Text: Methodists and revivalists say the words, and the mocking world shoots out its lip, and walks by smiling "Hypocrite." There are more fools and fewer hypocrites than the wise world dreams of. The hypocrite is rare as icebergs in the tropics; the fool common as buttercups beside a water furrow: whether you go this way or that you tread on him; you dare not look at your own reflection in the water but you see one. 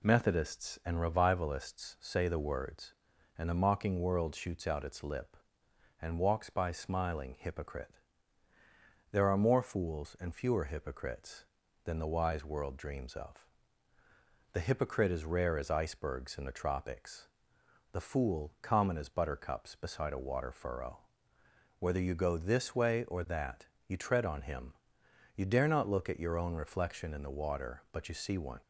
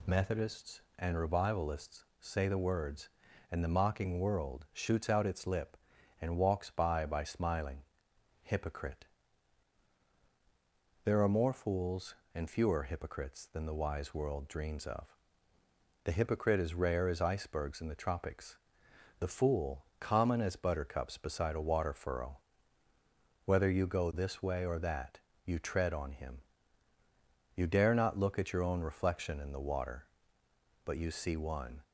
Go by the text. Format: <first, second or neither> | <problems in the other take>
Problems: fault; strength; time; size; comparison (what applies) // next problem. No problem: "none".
first | pauses between "revivalists" and "say"; slight; at 2.0 s; 0.16 s long // says "by" twice; at 7.0 s // pauses between "smiling" and "Hypocrite"; noticeable; at 7.8 s; 0.60 s long // pauses between "that" and "you"; slight; at 25.2 s; 0.24 s long; slight in the first